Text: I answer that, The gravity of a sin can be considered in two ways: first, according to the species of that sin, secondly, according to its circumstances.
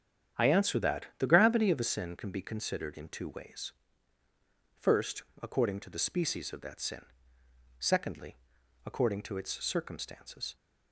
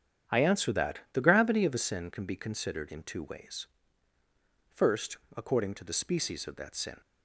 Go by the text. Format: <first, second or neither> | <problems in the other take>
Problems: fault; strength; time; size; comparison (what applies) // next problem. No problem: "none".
first | starts louder than the rest; strong; until 1.4 s; 8.5 dB; strong in the first // stops before "secondly according to its circumstances"; at 7.0 s